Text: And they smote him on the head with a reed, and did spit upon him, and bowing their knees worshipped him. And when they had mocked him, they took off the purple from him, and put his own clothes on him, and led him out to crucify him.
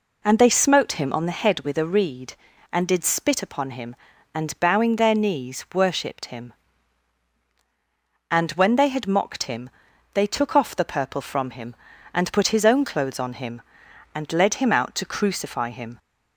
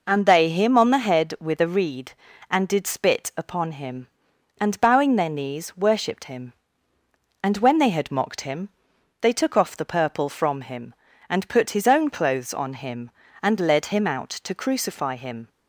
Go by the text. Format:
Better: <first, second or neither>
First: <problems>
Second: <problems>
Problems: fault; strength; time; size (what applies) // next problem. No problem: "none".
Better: first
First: none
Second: skips "smote"; at 0.4 s